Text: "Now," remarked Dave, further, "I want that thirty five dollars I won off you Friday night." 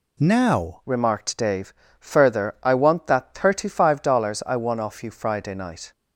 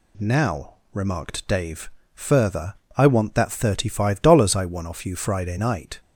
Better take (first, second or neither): second